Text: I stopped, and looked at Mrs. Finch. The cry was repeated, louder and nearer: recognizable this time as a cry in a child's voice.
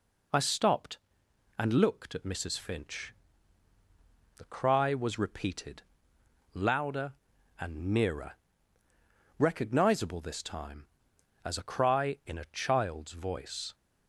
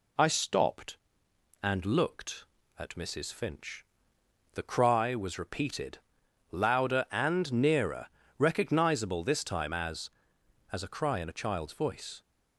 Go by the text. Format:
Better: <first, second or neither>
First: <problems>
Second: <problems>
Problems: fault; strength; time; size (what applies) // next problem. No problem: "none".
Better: first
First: none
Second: says "as" twice; at 10.7 s